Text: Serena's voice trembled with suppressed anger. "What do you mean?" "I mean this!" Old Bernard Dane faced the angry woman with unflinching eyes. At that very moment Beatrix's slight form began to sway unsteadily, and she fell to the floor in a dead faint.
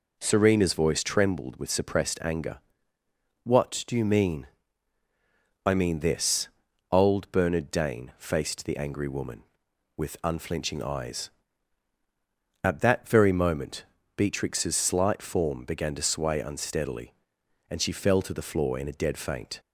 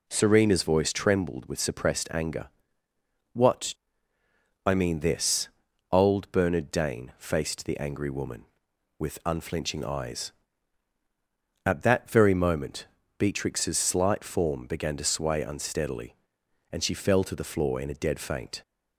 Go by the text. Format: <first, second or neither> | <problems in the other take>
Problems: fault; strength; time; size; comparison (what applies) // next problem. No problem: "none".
first | skips "do you mean"; at 4.1 s // pauses between "moment" and "Beatrix's"; slight; at 12.8 s; 0.32 s long; slight in the first